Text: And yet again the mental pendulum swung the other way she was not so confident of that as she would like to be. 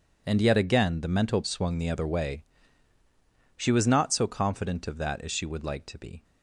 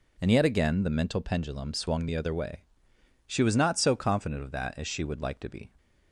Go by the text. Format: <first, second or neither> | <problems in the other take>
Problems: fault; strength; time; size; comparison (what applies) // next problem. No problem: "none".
second | skips "pendulum"; at 1.4 s // pauses between "way" and "she"; at 2.4 s; 1.1 s long; noticeable in the second